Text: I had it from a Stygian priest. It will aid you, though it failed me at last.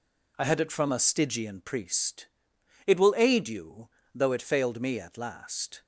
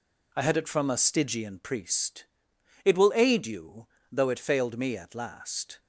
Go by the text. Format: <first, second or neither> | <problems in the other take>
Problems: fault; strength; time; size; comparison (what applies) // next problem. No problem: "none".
neither | none